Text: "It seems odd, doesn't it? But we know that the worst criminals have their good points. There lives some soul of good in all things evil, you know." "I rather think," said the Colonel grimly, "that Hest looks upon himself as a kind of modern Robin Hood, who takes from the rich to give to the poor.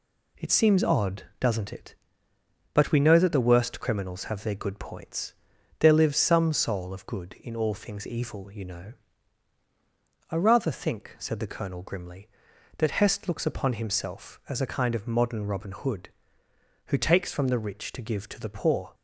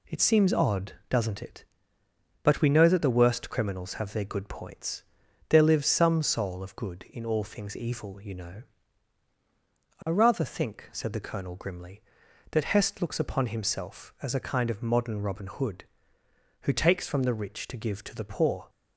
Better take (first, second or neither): neither